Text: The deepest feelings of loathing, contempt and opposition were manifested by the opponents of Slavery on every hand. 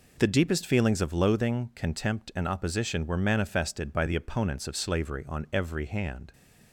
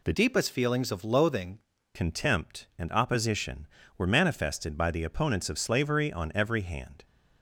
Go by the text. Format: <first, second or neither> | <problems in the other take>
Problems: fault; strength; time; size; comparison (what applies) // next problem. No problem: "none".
first | changes voice from "deepest" to "loathing"; from 0.1 to 1.6 s; 1.5 s long